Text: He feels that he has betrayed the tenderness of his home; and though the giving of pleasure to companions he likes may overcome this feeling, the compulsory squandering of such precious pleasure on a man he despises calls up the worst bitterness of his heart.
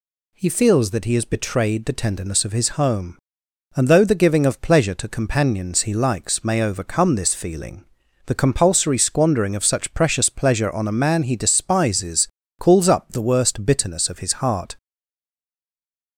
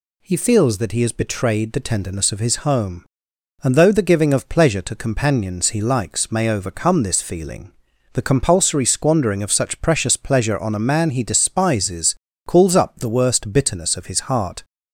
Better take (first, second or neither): second